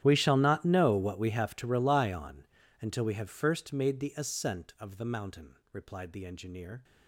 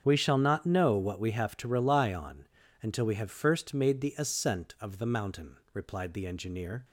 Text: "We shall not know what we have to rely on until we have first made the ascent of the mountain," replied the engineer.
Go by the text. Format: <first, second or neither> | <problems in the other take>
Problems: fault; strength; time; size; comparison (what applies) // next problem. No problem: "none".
second | gets quieter; strong; throughout; 22 dB // starts louder than the rest; strong; until 1.0 s; 11 dB; also in the second // pauses between "on" and "until"; slight; at 2.4 s; 0.36 s long; slight in the second